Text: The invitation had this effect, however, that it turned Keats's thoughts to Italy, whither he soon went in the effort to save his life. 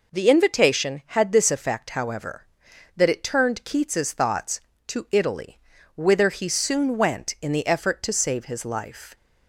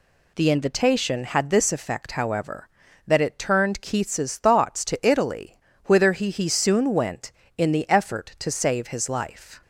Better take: first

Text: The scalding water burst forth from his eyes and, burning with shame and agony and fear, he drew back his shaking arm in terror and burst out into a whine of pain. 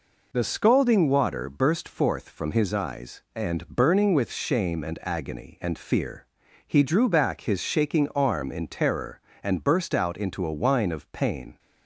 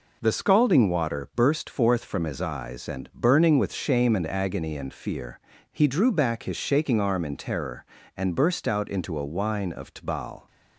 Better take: first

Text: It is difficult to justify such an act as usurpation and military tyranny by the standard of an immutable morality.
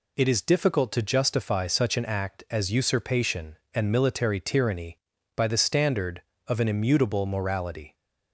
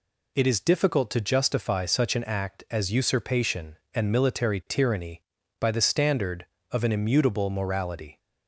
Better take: neither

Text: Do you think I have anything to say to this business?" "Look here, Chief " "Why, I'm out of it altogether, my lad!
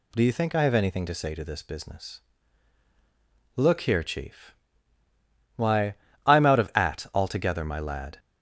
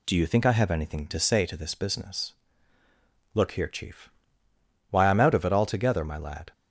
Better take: second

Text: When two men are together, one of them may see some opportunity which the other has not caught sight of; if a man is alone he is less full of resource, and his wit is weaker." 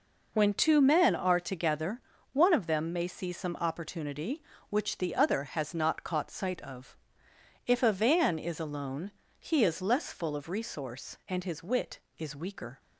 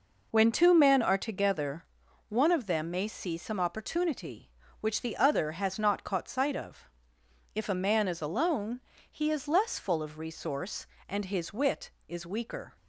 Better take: second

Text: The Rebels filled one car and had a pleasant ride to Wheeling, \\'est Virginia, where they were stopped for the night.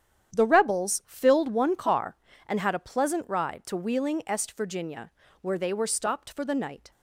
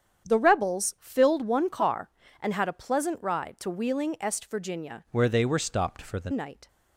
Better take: first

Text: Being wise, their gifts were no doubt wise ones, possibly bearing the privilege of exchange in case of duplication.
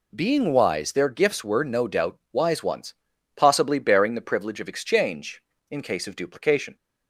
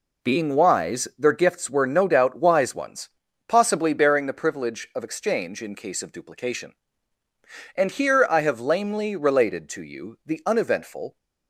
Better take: first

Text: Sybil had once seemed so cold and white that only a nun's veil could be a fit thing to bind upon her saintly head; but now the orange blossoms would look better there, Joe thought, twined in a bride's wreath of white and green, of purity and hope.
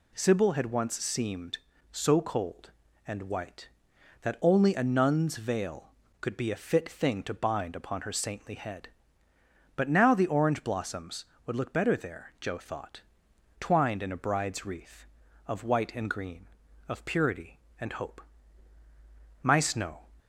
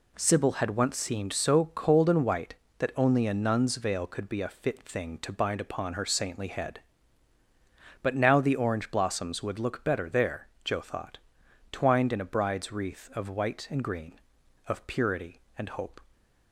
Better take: second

